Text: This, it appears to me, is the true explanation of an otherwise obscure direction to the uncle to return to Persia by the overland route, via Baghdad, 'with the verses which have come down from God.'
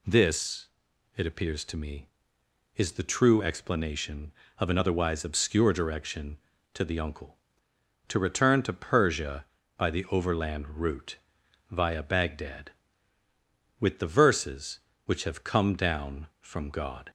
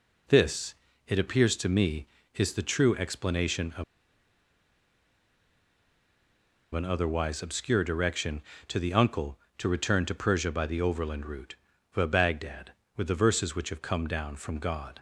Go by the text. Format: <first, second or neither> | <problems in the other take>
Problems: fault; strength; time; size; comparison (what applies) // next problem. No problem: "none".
first | pauses between "of" and "an"; strong; at 3.8 s; 2.9 s long